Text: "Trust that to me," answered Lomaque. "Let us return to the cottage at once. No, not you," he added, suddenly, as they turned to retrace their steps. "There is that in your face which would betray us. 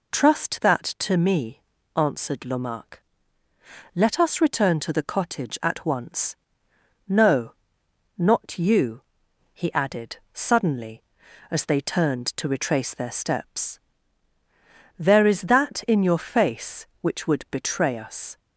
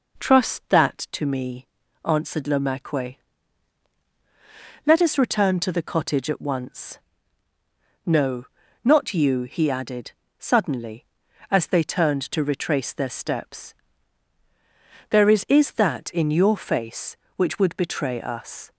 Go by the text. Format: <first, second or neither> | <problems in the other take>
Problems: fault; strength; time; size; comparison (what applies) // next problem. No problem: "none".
first | says "is" twice; at 15.4 s